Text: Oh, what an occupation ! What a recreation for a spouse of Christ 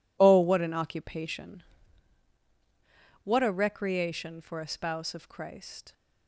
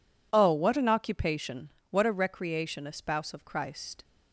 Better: first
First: none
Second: skips "for"; at 2.8 s

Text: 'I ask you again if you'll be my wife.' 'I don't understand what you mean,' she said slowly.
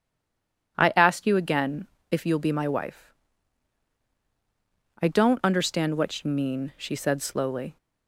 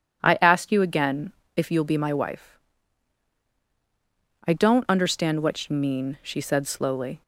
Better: second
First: stays silent before the first word; slight; until 0.7 s; 0.7 s long // pauses between "again" and "if"; slight; at 1.8 s; 0.24 s long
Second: pauses between "again" and "if"; slight; at 1.3 s; 0.24 s long

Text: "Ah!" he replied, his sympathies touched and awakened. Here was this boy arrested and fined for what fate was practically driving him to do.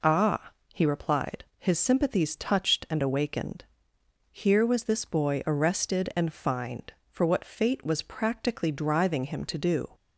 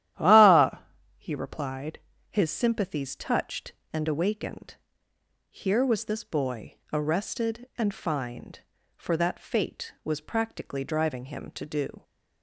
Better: first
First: none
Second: starts louder than the rest; strong; until 1.5 s; 12 dB // pauses between "boy" and "arrested"; slight; at 6.7 s; 0.18 s long // says "that" for "what"; at 9.1 s

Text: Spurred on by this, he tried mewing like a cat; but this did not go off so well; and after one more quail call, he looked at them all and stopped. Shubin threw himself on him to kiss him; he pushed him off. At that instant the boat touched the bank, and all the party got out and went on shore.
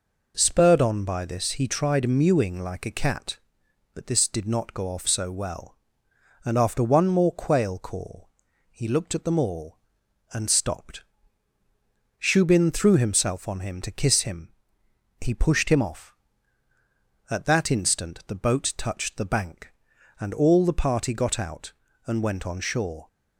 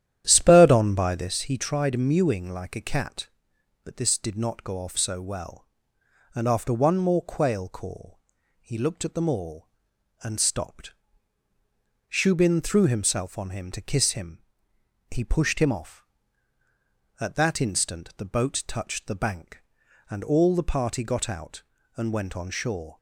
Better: first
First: none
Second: starts louder than the rest; strong; until 1.4 s; 11 dB

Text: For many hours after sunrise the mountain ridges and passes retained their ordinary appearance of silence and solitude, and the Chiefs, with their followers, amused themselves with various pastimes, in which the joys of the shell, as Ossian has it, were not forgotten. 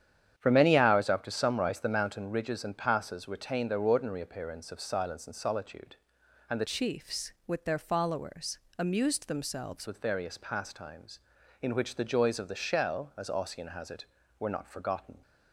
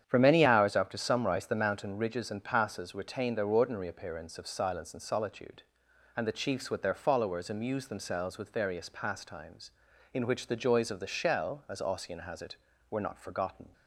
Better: second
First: starts louder than the rest; strong; until 1.3 s; 9 dB // changes voice from "Chiefs" to "themselves"; from 6.6 to 9.8 s; 3.2 s long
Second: starts louder than the rest; strong; until 1.0 s; 9 dB

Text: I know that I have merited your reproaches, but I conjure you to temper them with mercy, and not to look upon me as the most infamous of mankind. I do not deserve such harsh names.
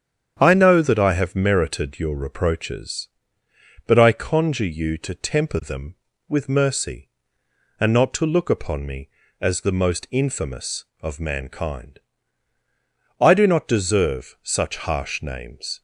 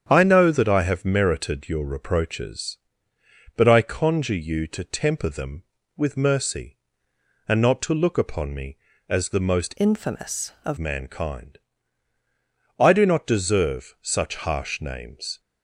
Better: first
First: starts louder than the rest; strong; until 1.4 s; 8.5 dB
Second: starts louder than the rest; strong; until 1.1 s; 8.5 dB // changes voice from "infamous" to "of"; from 9.7 to 10.7 s; 1.0 s long

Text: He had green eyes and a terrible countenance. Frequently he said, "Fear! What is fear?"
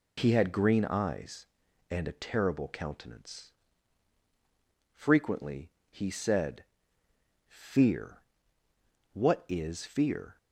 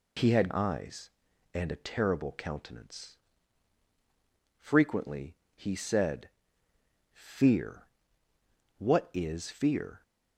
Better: first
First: pauses between "Frequently" and "he"; slight; at 5.6 s; 0.22 s long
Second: skips "green"; at 0.4 s // pauses between "Frequently" and "he"; slight; at 5.3 s; 0.22 s long

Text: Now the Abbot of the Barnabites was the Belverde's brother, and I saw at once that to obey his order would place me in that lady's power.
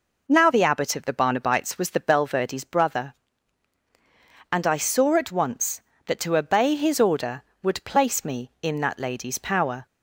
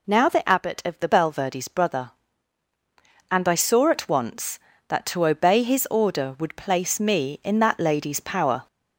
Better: first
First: none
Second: skips "Barnabites was the"; at 1.0 s

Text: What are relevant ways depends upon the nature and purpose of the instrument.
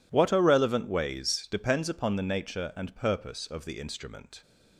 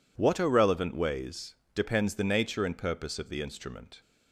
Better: first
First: none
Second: pauses between "ways" and "depends"; slight; at 1.5 s; 0.18 s long // skips "upon"; at 2.1 s

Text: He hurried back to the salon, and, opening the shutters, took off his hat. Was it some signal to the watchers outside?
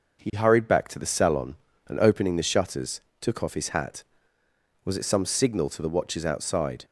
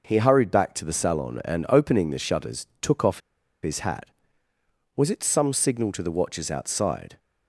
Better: first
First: none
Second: pauses between "off" and "his"; at 3.1 s; 0.43 s long

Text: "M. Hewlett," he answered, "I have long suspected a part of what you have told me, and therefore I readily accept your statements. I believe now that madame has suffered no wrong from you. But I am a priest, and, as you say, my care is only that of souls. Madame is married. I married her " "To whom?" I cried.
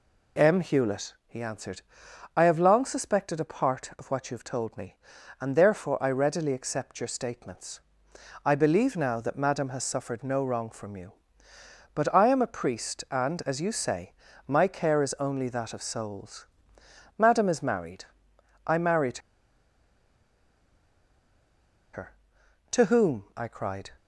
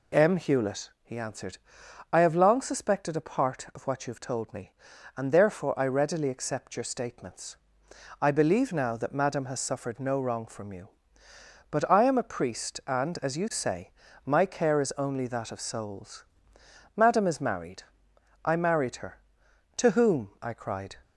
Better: second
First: pauses between "married" and "her"; strong; at 19.1 s; 2.7 s long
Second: none

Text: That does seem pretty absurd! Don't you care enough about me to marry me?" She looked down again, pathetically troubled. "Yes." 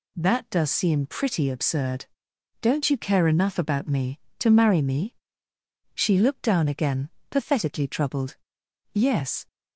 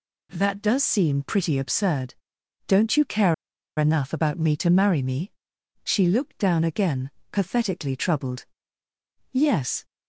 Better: first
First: none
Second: pauses between "care" and "enough"; at 3.3 s; 0.44 s long

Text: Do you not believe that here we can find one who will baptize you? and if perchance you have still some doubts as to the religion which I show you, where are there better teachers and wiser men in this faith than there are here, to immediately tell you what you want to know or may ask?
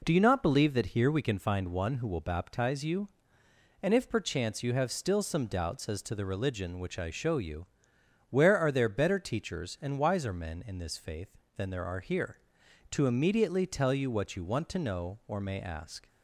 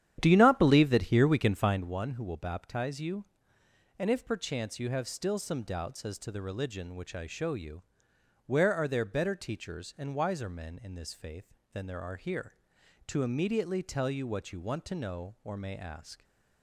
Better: first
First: none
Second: starts louder than the rest; strong; until 1.9 s; 10.5 dB

